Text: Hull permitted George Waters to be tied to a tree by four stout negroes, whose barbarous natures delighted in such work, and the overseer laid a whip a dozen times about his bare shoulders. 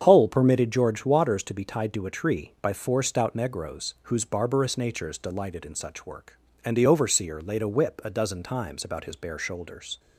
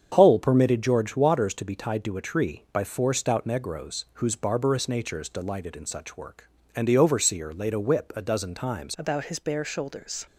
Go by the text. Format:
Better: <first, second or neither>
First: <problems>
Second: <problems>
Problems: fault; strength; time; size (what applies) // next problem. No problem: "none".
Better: first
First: starts louder than the rest; strong; until 1.0 s; 7.5 dB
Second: starts louder than the rest; strong; until 1.1 s; 7.5 dB // changes voice at "about"; from 8.9 s on; 1.3 s long